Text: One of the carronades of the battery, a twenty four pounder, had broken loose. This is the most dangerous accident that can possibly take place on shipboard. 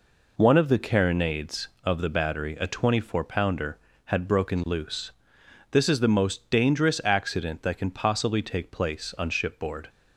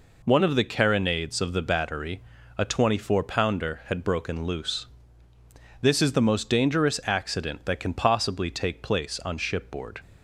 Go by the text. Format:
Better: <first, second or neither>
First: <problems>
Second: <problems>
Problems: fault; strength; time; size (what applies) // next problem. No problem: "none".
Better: neither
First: none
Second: none